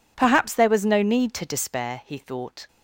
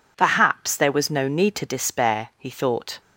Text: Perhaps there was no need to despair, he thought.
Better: neither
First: none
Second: none

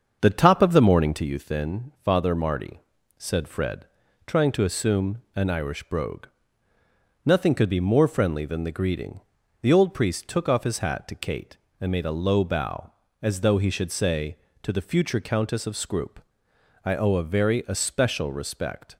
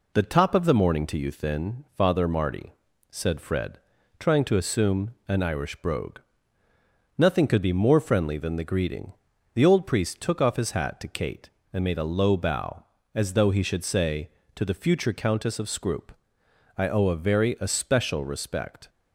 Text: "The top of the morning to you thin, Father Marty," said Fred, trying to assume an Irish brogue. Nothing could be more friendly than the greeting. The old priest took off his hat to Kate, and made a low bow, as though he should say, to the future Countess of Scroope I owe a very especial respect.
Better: second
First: starts louder than the rest; until 1.3 s; 6.5 dB // pauses between "Scroope" and "I"; noticeable; at 16.2 s; 0.60 s long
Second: pauses between "Scroope" and "I"; noticeable; at 16.1 s; 0.60 s long

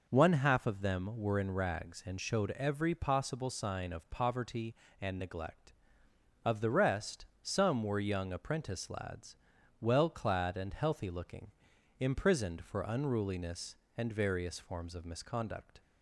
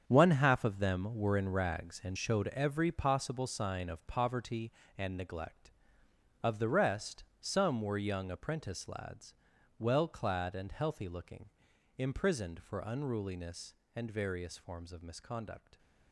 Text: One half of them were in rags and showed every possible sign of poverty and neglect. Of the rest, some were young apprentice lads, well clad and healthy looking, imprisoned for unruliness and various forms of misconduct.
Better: first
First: none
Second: gets quieter; strong; throughout; 11 dB

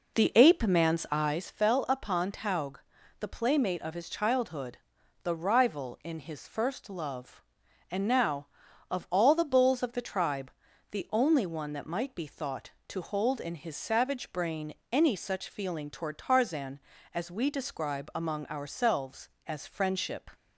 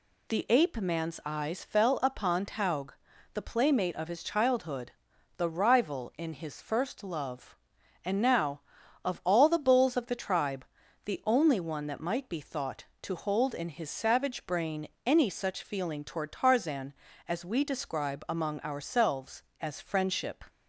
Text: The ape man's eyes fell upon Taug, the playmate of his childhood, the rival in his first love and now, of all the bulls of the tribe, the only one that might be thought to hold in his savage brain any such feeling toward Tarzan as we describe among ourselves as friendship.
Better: second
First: starts louder than the rest; noticeable; until 1.5 s; 4.5 dB // pauses between "brain" and "any"; slight; at 14.7 s; 0.18 s long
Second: pauses between "brain" and "any"; slight; at 14.8 s; 0.18 s long

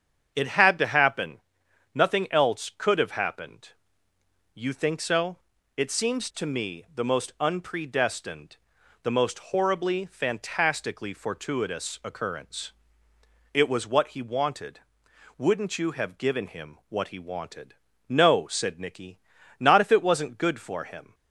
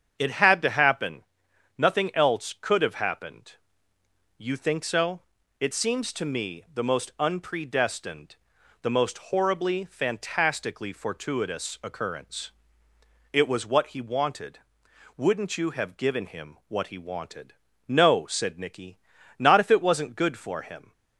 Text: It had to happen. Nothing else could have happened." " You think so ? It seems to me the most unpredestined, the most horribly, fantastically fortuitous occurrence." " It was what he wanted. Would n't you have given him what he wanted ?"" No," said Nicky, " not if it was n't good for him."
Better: neither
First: starts louder than the rest; strong; until 1.3 s; 8 dB // pauses between "most" and "horribly"; slight; at 9.3 s; 0.16 s long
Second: starts louder than the rest; strong; until 1.2 s; 8 dB // pauses between "most" and "horribly"; slight; at 9.1 s; 0.16 s long

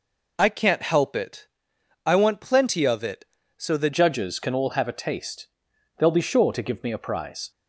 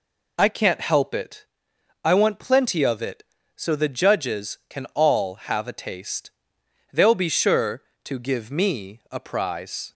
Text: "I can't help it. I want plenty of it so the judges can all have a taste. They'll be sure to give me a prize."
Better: second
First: changes voice at "judges"; from 3.9 s on; 3.6 s long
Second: none

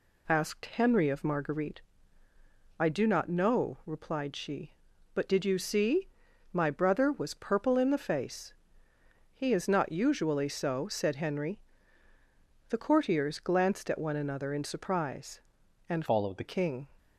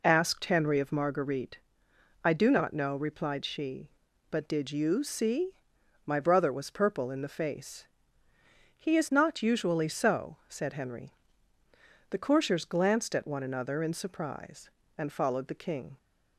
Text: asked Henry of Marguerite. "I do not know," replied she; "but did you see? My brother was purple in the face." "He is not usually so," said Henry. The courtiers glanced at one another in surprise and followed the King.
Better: second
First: changes voice from "followed" to "the"; from 16.0 to 16.4 s; 0.4 s long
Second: none

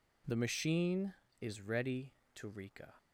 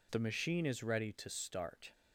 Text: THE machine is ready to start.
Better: second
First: says "rika" for "start"; at 2.4 s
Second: none

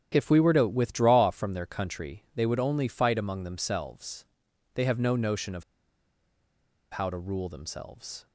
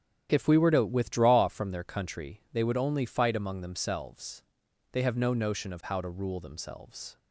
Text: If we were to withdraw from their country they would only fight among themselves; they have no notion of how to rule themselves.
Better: second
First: starts louder than the rest; strong; until 1.1 s; 9.5 dB // pauses between "of" and "how"; strong; at 5.6 s; 1.2 s long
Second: starts louder than the rest; strong; until 1.3 s; 9.5 dB

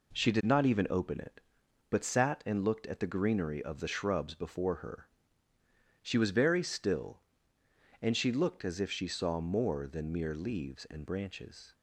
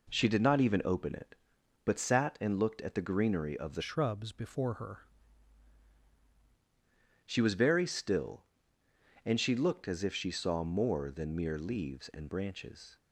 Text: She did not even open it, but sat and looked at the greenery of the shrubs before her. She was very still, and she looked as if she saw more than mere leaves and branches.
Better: first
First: none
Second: changes voice from "shrubs" to "her"; from 3.8 to 4.9 s; 1.1 s long

